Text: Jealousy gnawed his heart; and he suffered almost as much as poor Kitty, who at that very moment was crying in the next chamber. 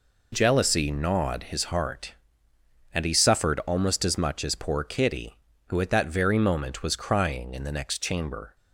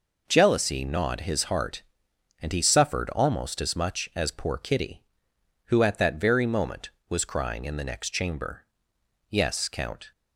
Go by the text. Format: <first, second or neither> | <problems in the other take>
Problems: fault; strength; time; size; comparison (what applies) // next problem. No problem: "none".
first | goes on to say "Yes Count"; noticeable; from 9.2 s on; 0.82 s long